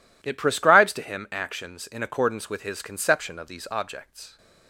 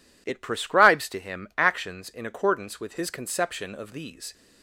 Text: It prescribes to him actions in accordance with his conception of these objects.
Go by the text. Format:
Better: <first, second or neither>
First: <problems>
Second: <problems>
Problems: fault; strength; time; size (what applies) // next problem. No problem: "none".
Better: first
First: none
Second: stops before "objects"; at 4.3 s